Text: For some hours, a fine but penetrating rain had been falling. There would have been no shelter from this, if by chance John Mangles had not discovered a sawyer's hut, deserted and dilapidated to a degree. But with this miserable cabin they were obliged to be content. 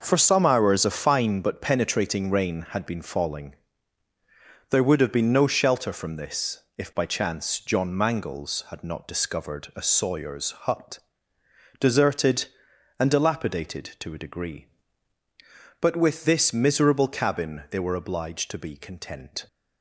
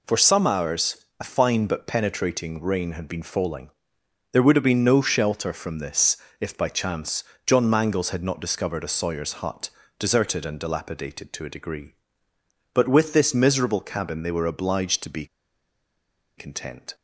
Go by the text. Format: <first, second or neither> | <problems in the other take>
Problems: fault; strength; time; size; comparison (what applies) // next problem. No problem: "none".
first | pauses between "chance" and "John"; slight; at 7.2 s; 0.24 s long // pauses between "be" and "content"; at 15.2 s; 1.1 s long